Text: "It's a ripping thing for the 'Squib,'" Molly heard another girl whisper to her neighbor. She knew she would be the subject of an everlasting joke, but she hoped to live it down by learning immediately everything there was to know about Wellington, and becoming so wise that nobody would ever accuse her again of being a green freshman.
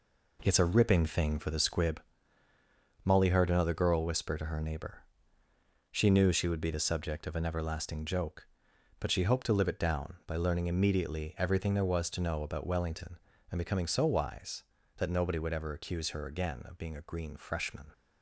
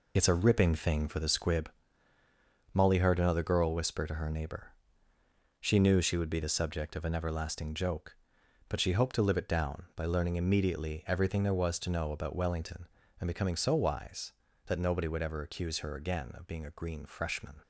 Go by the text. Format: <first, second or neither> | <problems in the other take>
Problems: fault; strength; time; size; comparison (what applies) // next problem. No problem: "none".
first | loses the start of "It's"; at 0.1 s; 65 ms